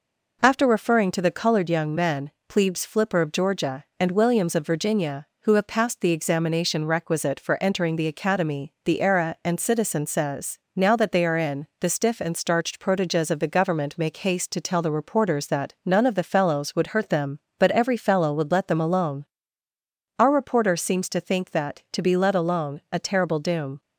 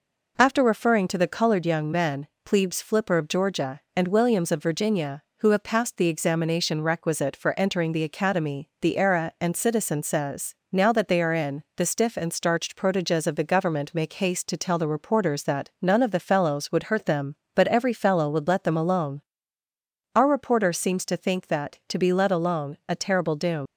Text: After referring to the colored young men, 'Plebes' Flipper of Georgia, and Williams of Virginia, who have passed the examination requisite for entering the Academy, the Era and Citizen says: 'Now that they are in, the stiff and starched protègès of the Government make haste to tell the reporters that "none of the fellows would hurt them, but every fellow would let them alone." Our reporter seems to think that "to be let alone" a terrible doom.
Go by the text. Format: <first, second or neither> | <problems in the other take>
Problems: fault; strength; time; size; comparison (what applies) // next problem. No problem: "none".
first | leaves "doom" unfinished; at 23.6 s; 115 ms